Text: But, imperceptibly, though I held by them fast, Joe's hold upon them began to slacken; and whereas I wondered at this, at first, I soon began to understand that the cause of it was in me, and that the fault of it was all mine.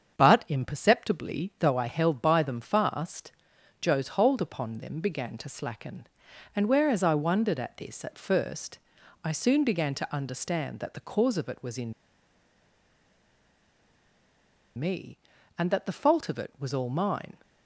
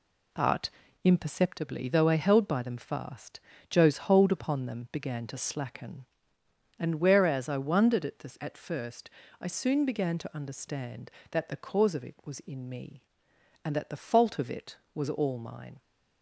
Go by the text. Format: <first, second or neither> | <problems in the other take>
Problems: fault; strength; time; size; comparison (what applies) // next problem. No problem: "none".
second | starts louder than the rest; strong; until 1.2 s; 7.5 dB // pauses between "in" and "me"; strong; at 11.9 s; 2.8 s long